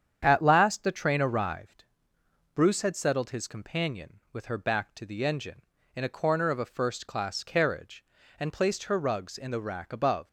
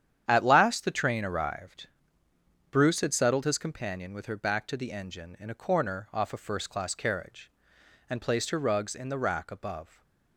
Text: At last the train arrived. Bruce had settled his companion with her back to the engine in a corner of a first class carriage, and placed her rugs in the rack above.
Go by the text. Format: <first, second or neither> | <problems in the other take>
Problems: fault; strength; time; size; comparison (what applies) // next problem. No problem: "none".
first | starts louder than the rest; strong; until 1.2 s; 9.5 dB; strong in the first // says "off" for "of"; at 6.1 s // stays silent after the last word; slight; from 9.8 s on; 0.5 s long